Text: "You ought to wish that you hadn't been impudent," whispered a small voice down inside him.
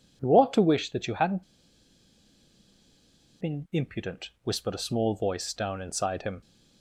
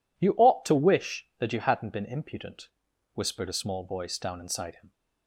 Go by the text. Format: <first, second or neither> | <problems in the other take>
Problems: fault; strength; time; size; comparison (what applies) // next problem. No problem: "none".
second | pauses between "hadn't" and "been"; strong; at 1.4 s; 1.9 s long